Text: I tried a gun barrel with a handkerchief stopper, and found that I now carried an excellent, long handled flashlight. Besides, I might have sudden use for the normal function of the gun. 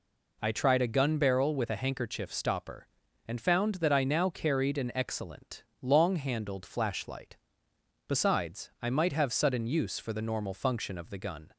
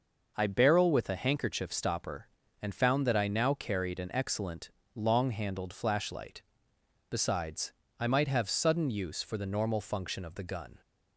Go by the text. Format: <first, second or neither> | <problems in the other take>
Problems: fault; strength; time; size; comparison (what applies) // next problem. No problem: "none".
first | skips "tried a gun"; at 0.4 s